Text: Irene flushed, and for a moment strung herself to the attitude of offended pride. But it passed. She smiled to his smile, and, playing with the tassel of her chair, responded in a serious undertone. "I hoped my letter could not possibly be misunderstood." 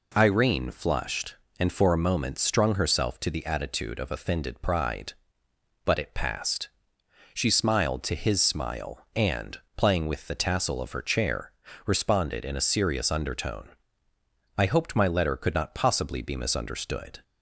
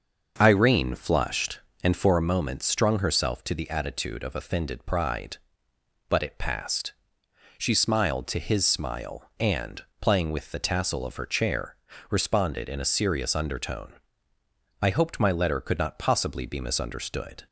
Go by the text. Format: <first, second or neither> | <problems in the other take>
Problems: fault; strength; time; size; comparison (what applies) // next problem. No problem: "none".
first | starts louder than the rest; until 2.2 s; 6.5 dB